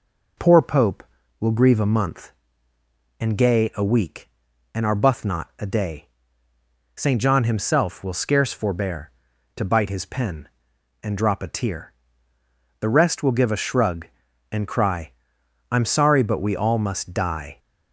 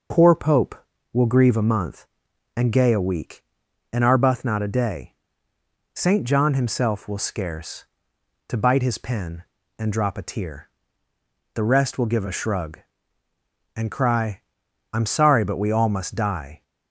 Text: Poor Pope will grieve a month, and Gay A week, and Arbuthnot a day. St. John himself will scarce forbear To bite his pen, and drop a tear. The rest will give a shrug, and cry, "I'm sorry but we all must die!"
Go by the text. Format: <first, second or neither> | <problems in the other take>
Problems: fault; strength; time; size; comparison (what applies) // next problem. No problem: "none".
first | skips "forbear"; at 8.1 s